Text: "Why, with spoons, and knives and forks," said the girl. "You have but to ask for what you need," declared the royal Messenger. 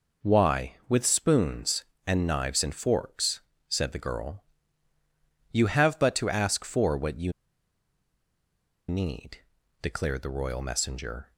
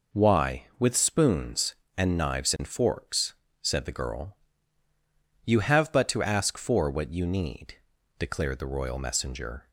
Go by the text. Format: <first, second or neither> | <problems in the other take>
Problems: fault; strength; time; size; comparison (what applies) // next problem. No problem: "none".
second | pauses between "you" and "need"; strong; at 7.3 s; 1.5 s long